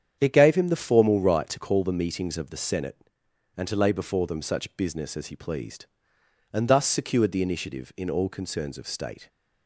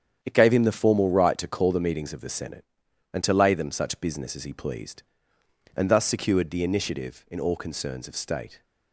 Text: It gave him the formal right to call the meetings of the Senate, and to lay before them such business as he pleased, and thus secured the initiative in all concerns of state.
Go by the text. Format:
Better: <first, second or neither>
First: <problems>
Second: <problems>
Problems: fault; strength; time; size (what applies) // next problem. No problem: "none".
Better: first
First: starts louder than the rest; strong; until 1.2 s; 8.5 dB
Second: starts louder than the rest; strong; until 1.2 s; 8.5 dB // skips "before"; at 3.5 s